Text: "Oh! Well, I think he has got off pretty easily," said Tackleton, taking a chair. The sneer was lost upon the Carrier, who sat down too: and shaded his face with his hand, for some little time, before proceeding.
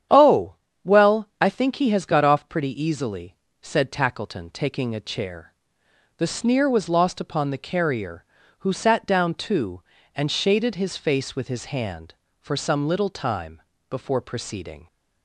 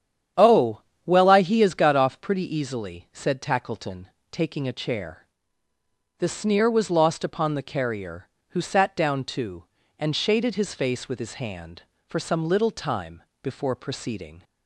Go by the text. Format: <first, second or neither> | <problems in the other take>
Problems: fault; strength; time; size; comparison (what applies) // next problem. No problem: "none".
first | starts louder than the rest; strong; until 1.6 s; 9 dB; strong in the first // skips "think"; at 1.4 s